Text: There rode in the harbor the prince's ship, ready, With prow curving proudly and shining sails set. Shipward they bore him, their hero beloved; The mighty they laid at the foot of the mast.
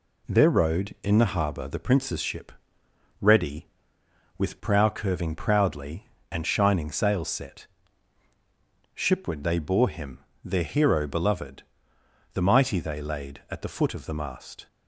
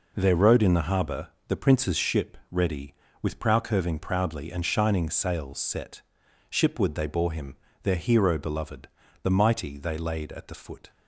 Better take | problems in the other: first | pauses between "harbor" and "the"; slight; at 1.2 s; 0.22 s long // stops before "of the mast"; at 10.9 s

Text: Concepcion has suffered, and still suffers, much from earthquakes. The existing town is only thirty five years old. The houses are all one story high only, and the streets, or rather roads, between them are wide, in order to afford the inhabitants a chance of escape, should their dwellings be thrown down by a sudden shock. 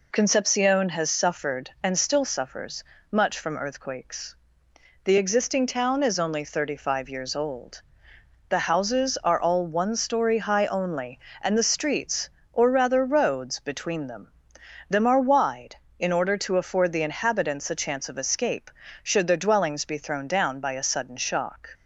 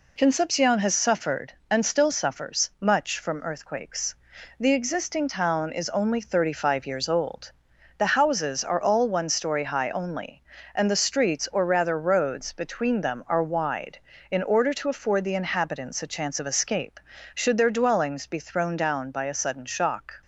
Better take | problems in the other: second | says "them" twice; at 14.8 s

